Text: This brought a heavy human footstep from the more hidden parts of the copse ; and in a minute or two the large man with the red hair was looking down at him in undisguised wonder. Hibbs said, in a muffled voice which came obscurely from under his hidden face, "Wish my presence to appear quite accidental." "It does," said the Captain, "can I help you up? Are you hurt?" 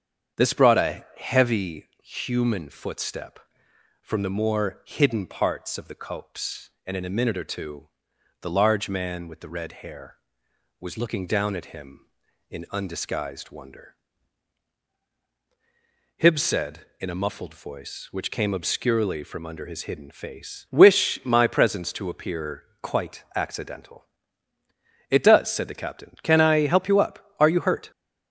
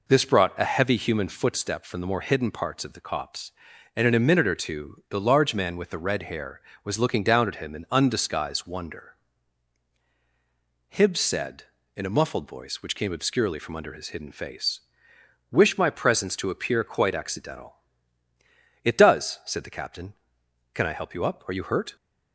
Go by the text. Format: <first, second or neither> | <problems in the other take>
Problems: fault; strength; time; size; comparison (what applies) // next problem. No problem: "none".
second | starts louder than the rest; strong; until 2.1 s; 7.5 dB // pauses between "two" and "the"; noticeable; at 7.8 s; 0.52 s long // pauses between "appear" and "quite"; slight; at 22.6 s; 0.16 s long